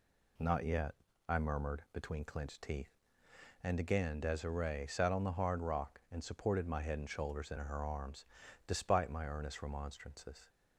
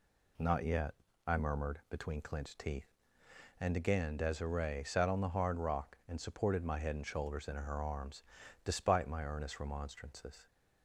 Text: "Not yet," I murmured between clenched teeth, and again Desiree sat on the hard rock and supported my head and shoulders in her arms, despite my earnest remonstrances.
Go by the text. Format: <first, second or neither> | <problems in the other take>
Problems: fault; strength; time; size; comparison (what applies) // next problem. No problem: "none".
neither | none